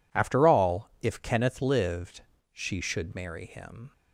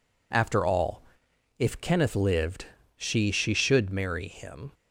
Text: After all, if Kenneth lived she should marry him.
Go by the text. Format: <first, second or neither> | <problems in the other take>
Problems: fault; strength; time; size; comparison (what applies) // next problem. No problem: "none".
first | pauses between "lived" and "she"; slight; at 2.6 s; 0.32 s long; slight in the first // says "she" twice; at 3.3 s